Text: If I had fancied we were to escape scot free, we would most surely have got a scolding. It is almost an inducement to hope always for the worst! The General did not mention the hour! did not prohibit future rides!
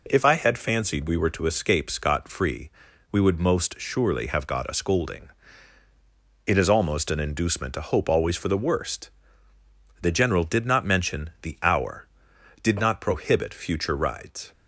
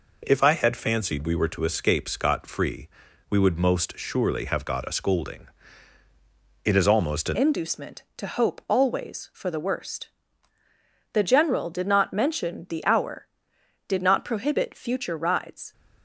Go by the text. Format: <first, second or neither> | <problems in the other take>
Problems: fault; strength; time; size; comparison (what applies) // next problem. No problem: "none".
first | changes voice at "inducement"; from 7.3 s on; 8.4 s long